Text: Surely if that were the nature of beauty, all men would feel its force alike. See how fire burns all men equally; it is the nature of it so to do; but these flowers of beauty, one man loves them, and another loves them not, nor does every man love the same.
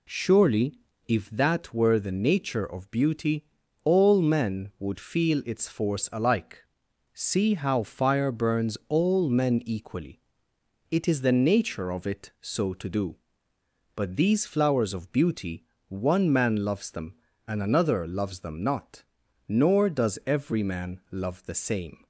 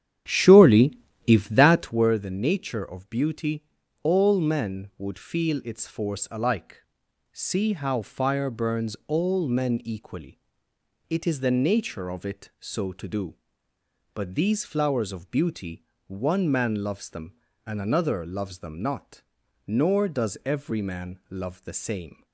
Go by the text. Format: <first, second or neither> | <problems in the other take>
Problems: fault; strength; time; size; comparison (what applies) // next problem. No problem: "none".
first | starts louder than the rest; strong; until 2.1 s; 9.5 dB // pauses between "Surely" and "if"; slight; at 0.9 s; 0.28 s long; slight in the first